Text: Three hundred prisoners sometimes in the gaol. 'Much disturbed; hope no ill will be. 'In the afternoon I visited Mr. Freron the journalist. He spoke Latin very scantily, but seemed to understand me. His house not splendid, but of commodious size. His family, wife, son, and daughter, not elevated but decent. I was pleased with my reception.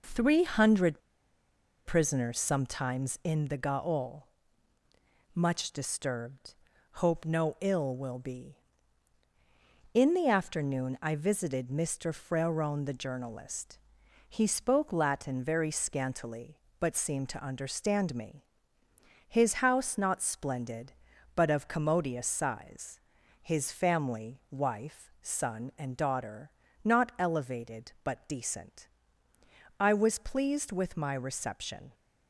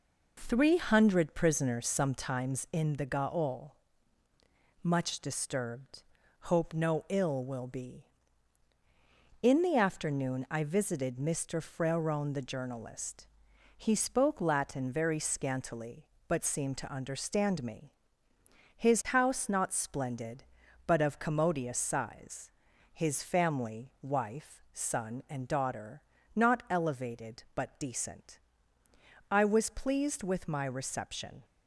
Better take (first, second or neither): second